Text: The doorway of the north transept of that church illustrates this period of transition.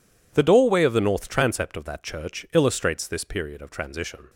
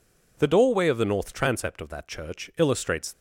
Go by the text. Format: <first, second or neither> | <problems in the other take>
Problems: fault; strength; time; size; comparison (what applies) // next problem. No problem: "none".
first | stops before "this period of transition"; at 3.1 s